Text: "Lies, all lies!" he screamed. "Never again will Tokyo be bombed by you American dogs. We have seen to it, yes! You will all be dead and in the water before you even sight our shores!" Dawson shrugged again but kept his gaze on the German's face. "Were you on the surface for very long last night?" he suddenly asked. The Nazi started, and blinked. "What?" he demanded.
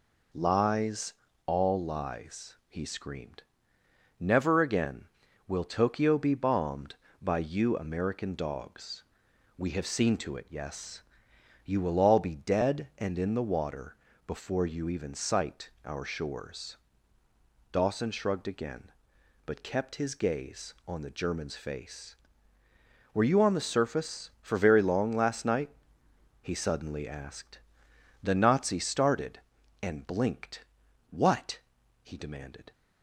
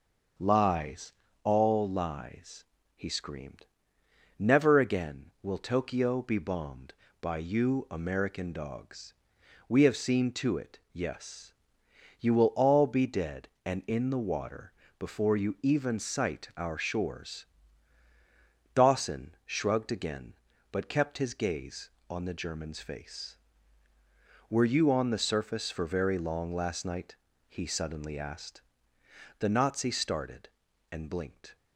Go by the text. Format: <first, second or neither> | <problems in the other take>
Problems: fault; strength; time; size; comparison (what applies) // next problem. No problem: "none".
first | pauses between "water" and "before"; slight; at 14.7 s; 0.26 s long; slight in the first // stops before "What he demanded"; at 31.5 s